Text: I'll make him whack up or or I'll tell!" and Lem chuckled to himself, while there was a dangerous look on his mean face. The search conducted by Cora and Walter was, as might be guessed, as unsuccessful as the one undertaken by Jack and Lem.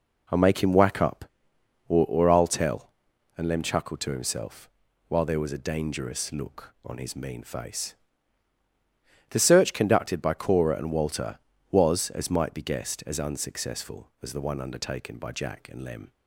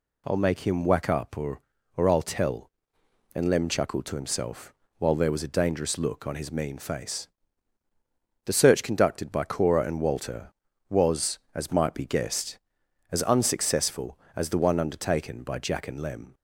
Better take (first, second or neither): neither